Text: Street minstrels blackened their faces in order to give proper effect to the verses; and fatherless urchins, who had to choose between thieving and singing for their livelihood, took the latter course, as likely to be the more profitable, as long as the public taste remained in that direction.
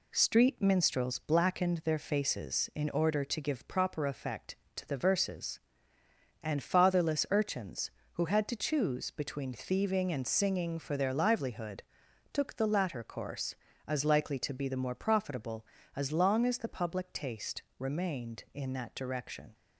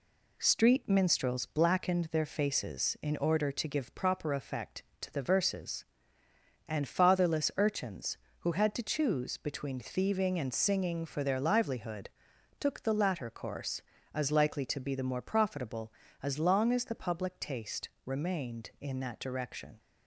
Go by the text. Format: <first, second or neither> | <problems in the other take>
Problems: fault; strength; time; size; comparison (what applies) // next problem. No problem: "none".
neither | pauses between "taste" and "remained"; slight; the same in both